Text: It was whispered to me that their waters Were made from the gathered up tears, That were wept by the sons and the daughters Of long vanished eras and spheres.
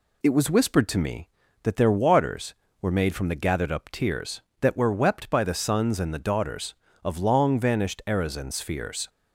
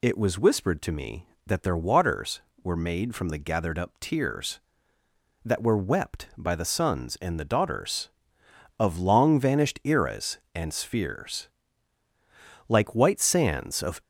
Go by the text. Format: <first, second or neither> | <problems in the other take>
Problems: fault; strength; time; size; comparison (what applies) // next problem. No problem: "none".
first | goes on to say "Like white sands of"; from 12.6 s on; 1.3 s long